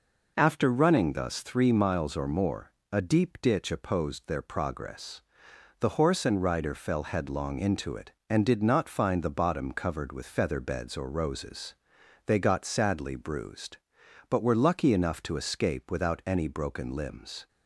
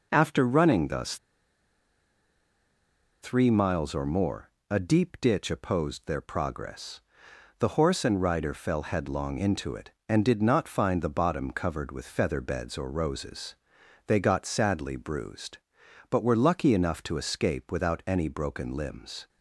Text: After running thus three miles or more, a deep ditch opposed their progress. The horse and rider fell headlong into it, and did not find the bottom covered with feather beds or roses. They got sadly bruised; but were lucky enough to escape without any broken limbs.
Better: first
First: none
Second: pauses between "thus" and "three"; strong; at 1.1 s; 2.0 s long

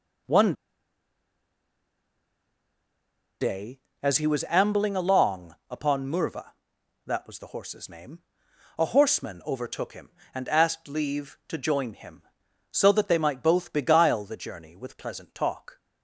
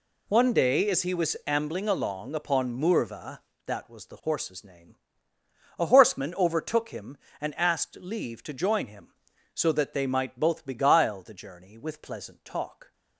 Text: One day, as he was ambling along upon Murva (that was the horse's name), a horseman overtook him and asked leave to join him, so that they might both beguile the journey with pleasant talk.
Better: second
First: pauses between "One" and "day"; strong; at 0.5 s; 2.8 s long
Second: none

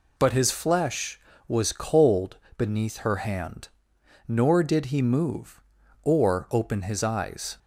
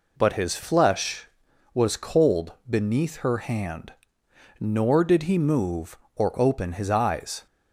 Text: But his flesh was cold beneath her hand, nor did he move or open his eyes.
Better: neither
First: pauses between "cold" and "beneath"; slight; at 2.3 s; 0.20 s long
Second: pauses between "cold" and "beneath"; slight; at 2.5 s; 0.16 s long

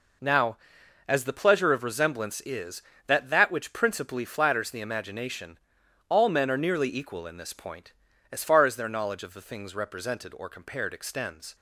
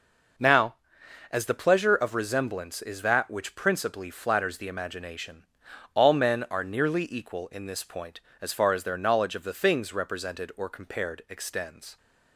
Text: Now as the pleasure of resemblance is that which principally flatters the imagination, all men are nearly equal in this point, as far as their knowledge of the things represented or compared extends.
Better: second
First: says "that" twice; at 3.2 s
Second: none

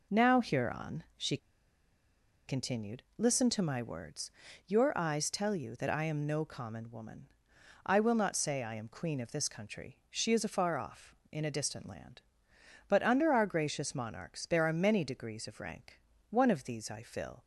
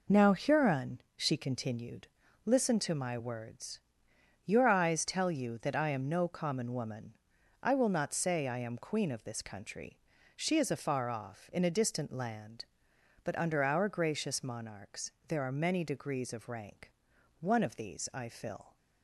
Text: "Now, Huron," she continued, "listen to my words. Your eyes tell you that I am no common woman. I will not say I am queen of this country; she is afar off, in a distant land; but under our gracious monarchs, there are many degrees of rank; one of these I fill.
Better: second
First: pauses between "she" and "continued"; at 1.3 s; 1.1 s long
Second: none

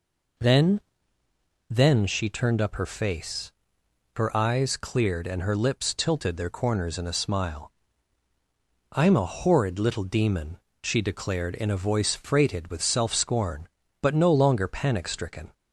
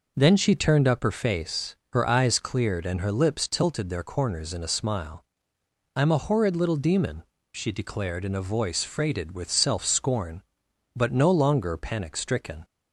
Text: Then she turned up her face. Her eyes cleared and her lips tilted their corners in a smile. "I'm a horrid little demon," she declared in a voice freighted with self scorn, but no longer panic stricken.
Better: second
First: says "Then" twice; at 1.6 s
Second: none

